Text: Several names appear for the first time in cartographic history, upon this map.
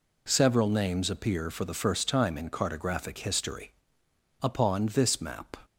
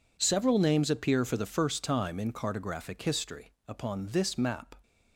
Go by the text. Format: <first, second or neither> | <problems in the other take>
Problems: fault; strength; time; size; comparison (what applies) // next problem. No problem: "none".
neither | none